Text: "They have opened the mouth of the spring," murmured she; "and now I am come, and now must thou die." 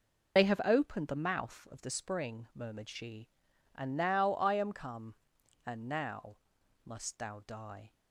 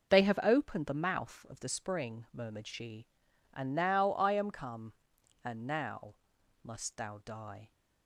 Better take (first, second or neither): second